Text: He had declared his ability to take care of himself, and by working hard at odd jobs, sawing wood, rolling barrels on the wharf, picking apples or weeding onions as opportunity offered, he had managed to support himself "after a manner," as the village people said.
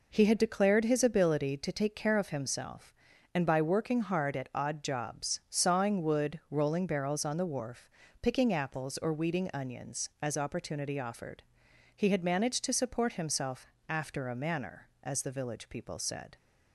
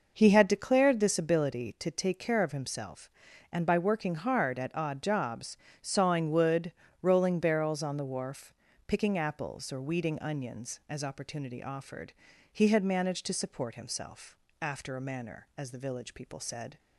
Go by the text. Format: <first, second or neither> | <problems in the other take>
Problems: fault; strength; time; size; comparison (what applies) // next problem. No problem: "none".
first | says "this" for "his"; at 0.9 s // pauses between "himself" and "after"; slight; at 14.3 s; 0.26 s long; slight in the first